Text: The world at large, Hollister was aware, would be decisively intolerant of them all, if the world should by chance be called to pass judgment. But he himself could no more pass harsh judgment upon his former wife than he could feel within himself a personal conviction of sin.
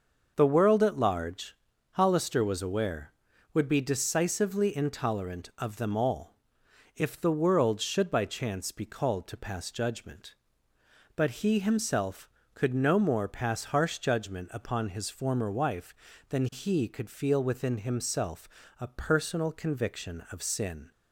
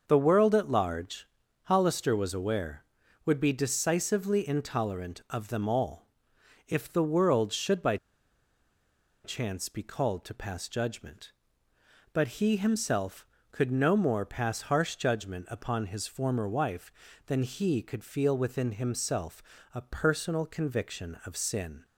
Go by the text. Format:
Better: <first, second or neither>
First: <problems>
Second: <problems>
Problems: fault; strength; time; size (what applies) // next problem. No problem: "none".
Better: first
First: starts louder than the rest; until 1.3 s; 6 dB // pauses between "himself" and "a"; slight; at 18.4 s; 0.32 s long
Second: starts louder than the rest; noticeable; until 1.0 s; 6 dB // pauses between "by" and "chance"; strong; at 7.9 s; 1.2 s long // pauses between "himself" and "a"; slight; at 19.4 s; 0.32 s long